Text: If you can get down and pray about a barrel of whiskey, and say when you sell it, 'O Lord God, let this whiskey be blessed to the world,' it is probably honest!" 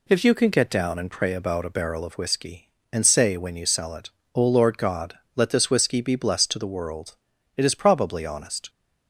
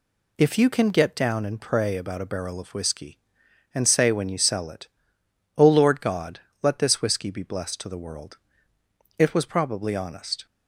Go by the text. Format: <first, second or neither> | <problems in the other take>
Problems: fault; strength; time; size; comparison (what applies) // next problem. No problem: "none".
first | says "was" for "is"; at 9.3 s